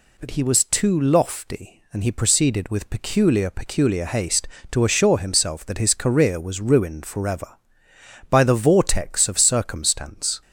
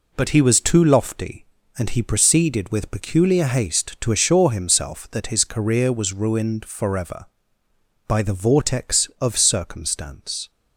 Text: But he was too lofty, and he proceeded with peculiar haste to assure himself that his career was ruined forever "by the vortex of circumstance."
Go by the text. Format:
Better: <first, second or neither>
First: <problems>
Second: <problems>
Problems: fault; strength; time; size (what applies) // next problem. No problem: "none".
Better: second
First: says "peculiar" twice; at 3.4 s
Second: none